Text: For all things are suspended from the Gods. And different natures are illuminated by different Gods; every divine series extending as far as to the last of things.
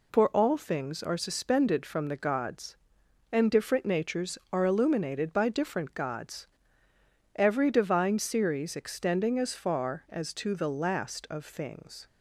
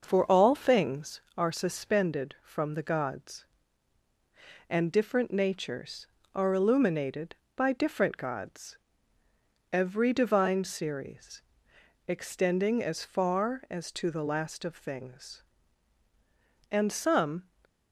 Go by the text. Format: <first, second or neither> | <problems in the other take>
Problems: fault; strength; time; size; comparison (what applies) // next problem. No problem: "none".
first | pauses between "series" and "extending"; noticeable; at 11.4 s; 0.64 s long // goes on to say "And some"; noticeable; from 16.7 s on; 0.72 s long